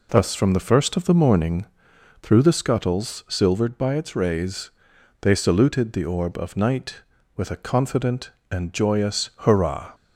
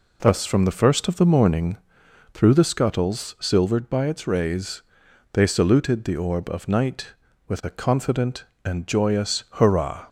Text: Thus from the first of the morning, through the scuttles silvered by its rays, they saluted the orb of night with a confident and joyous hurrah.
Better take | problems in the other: neither | none

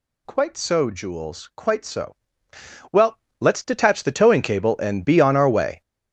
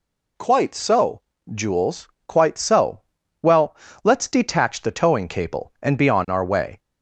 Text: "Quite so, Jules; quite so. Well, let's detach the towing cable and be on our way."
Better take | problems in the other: second | gets louder; strong; throughout; 11.5 dB

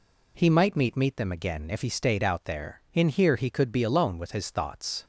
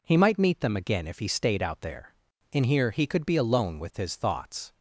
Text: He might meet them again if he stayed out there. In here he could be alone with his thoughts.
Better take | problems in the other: second | says "meet" twice; at 0.9 s

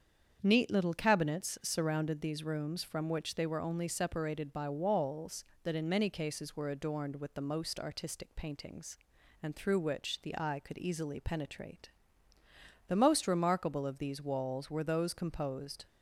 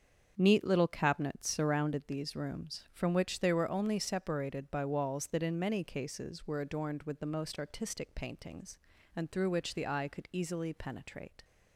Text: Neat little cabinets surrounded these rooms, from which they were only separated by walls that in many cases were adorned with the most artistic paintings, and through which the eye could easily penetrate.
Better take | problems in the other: second | starts louder than the rest; strong; until 1.4 s; 7.5 dB; also in the second // goes on to say "The most remarkable of these walls were those composed"; strong; from 12.8 s on; 2.9 s long

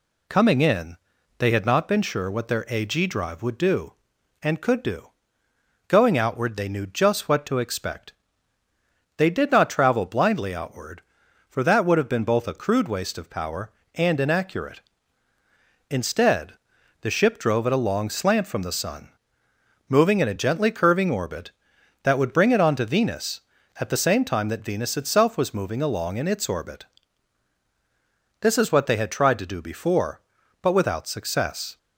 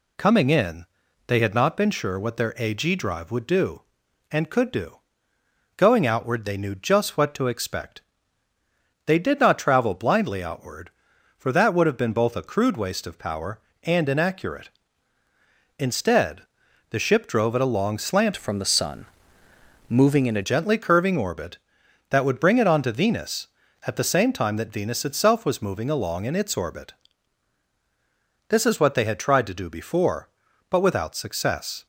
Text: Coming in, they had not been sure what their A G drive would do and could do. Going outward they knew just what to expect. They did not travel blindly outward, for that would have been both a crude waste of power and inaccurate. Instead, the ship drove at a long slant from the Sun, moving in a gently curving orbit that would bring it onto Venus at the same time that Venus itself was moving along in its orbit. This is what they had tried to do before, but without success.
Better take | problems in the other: first | changes voice from "from" to "a"; from 18.3 to 20.4 s; 2.1 s long

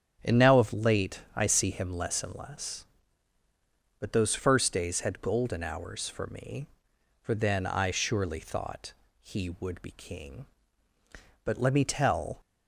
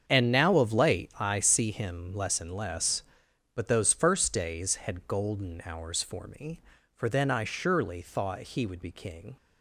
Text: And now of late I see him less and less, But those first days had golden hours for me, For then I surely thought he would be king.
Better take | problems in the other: second | starts louder than the rest; strong; until 1.3 s; 8.5 dB; strong in the second // pauses between "thought" and "he"; slight; at 8.9 s; 0.30 s long // goes on to say "But let me tell"; noticeable; from 11.4 s on; 0.96 s long

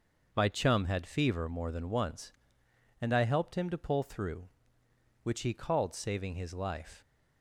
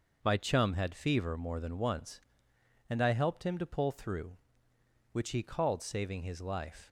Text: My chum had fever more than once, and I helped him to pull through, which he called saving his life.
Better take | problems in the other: neither | none

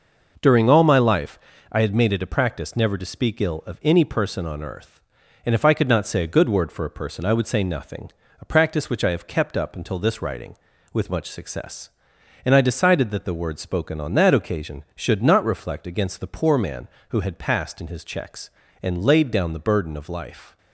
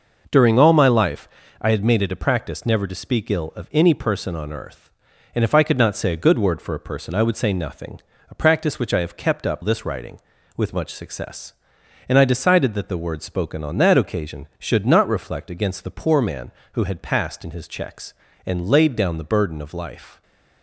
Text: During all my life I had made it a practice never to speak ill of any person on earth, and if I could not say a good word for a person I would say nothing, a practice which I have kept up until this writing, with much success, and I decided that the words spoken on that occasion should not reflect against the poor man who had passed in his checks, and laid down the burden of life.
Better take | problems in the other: first | pauses between "life" and "I"; slight; at 1.2 s; 0.34 s long; slight in the first // skips "until"; at 9.6 s

